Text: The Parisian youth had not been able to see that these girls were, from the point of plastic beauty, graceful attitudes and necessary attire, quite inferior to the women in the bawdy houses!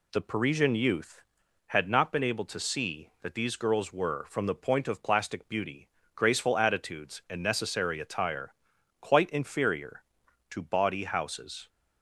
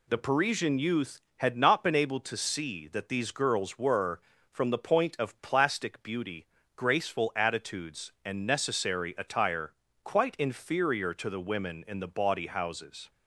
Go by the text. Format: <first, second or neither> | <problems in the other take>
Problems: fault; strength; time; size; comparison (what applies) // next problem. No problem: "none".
second | skips "the women in the"; at 10.6 s